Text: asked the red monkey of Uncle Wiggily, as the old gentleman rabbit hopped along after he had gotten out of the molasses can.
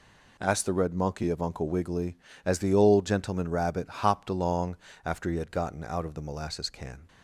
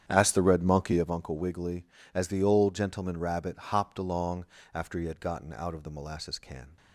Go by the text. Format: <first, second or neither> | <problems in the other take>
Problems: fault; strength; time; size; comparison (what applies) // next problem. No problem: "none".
first | starts louder than the rest; strong; until 1.2 s; 9 dB // pauses between "along" and "after"; slight; at 4.4 s; 0.30 s long; slight in the first